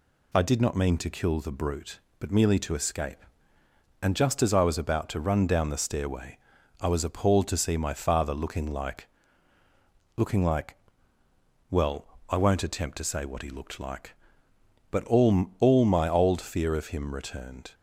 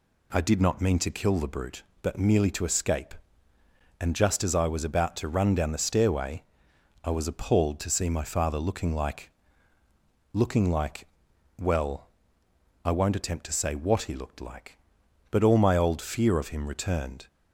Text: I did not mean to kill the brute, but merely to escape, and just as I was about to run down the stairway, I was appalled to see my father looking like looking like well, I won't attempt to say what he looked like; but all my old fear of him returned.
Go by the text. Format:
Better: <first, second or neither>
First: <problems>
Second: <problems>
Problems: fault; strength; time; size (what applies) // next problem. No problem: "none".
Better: second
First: pauses between "like" and "looking"; at 9.0 s; 1.1 s long // pauses between "like" and "well"; noticeable; at 10.7 s; 0.94 s long // says "all" twice; at 15.5 s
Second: pauses between "like" and "looking"; at 9.2 s; 1.0 s long // pauses between "like" and "well"; noticeable; at 11.0 s; 0.54 s long